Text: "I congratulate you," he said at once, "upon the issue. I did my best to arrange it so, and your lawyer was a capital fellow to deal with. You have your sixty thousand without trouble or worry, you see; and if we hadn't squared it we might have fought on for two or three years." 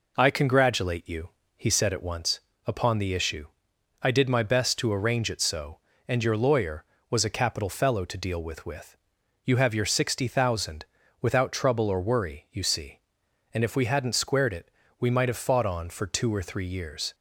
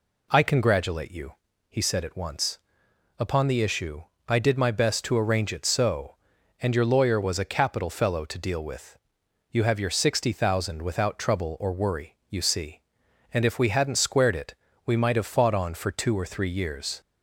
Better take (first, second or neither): second